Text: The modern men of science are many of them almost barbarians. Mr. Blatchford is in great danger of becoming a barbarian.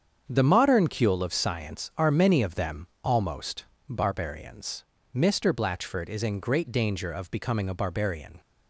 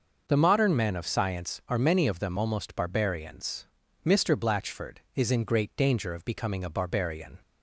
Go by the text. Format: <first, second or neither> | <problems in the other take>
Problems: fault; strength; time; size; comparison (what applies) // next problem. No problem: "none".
second | starts louder than the rest; strong; until 1.3 s; 7.5 dB // says "cule" for "men"; at 0.8 s // pauses between "them" and "almost"; slight; at 2.8 s; 0.16 s long // pauses between "almost" and "barbarians"; slight; at 3.6 s; 0.24 s long